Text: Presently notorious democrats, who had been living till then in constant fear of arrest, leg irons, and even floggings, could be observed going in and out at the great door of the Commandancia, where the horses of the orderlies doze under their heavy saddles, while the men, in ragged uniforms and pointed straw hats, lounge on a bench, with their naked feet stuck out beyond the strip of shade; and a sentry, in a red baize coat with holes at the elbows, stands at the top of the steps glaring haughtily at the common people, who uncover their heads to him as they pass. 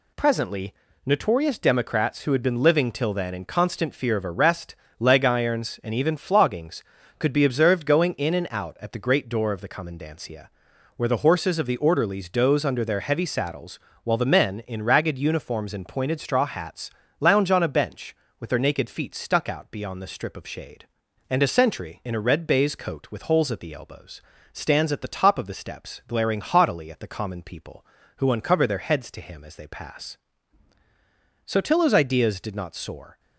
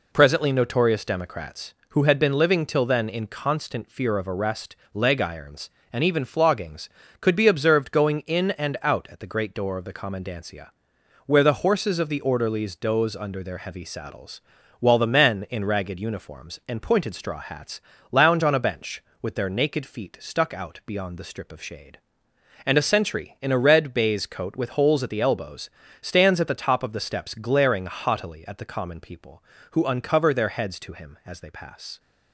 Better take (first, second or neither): second